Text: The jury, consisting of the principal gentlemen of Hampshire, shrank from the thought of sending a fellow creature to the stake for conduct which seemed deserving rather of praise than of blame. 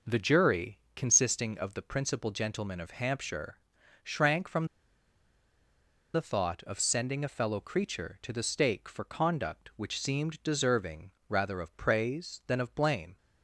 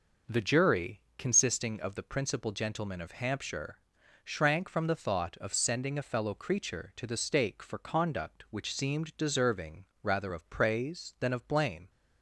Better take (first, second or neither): second